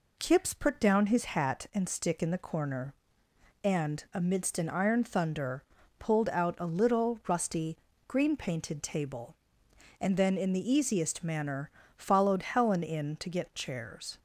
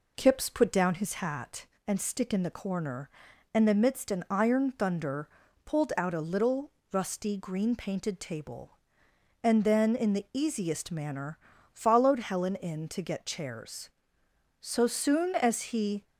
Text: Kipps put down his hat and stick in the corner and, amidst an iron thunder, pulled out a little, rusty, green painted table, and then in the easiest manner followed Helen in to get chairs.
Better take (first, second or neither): first